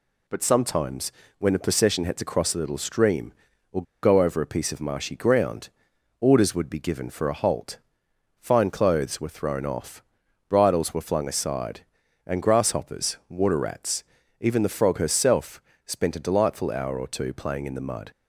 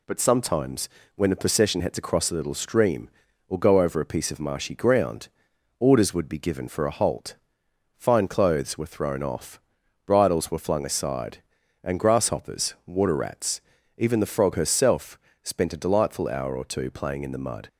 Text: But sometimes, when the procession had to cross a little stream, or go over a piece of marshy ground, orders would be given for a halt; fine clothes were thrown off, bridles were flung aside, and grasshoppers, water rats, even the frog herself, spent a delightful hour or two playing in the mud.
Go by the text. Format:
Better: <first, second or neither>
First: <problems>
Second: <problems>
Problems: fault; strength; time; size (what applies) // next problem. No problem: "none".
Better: second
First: pauses between "or" and "go"; slight; at 3.8 s; 0.19 s long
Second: none